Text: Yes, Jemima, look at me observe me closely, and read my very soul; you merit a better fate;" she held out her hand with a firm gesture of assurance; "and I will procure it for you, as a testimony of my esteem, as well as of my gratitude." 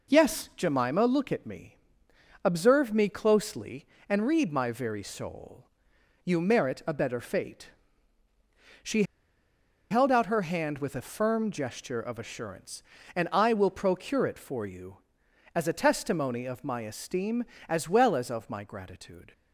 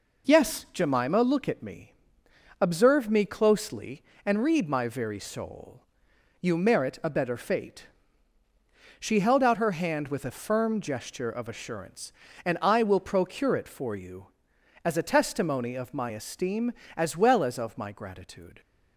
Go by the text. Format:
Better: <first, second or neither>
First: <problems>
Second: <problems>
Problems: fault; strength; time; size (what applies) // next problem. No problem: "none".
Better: second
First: pauses between "me" and "observe"; noticeable; at 1.7 s; 0.68 s long // pauses between "she" and "held"; noticeable; at 9.0 s; 0.87 s long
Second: pauses between "me" and "observe"; noticeable; at 1.9 s; 0.68 s long